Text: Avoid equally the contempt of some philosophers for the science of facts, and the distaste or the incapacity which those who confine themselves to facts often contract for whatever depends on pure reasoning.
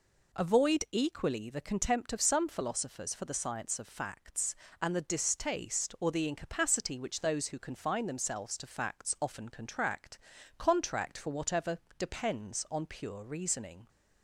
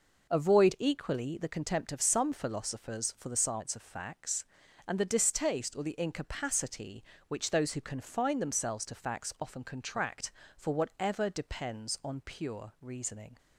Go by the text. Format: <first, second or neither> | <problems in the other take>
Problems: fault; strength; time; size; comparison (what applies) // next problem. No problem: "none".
second | says "contract" twice; at 10.5 s // pauses between "whatever" and "depends"; slight; at 11.7 s; 0.18 s long